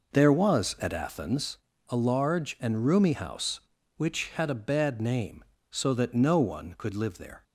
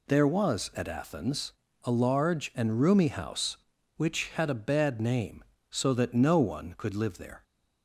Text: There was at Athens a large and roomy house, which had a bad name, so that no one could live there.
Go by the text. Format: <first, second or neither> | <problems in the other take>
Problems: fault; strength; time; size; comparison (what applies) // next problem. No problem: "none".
second | starts louder than the rest; noticeable; until 1.5 s; 5 dB // pauses between "Athens" and "a"; slight; at 1.5 s; 0.30 s long; slight in the second